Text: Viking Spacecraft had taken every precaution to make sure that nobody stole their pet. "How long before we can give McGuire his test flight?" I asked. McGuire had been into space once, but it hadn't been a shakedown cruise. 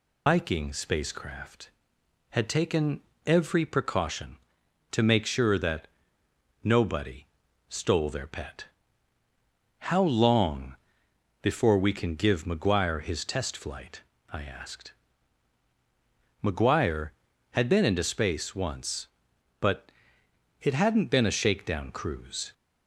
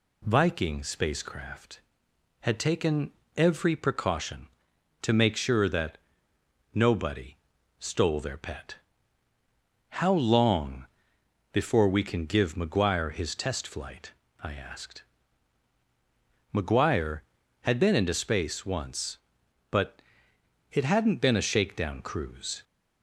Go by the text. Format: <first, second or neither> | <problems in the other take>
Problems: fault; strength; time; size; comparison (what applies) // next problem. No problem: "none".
second | loses the start of "Viking"; at 0.2 s; 145 ms // pauses between "taken" and "every"; slight; at 3.0 s; 0.24 s long; slight in the second // pauses between "that" and "nobody"; noticeable; at 5.8 s; 0.76 s long; noticeable in the second // pauses between "nobody" and "stole"; at 7.2 s; 0.42 s long; also in the second // pauses between "long" and "before"; noticeable; at 10.7 s; 0.66 s long; noticeable in the second // pauses between "but" and "it"; noticeable; at 19.9 s; 0.70 s long; noticeable in the second